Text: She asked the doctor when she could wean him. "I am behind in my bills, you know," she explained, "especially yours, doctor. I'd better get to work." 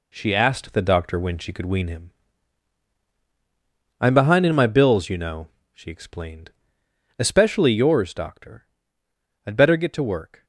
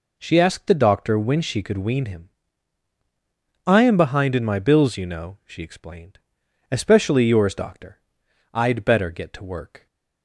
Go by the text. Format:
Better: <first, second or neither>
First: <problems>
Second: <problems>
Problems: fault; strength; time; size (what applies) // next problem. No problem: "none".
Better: neither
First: none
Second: none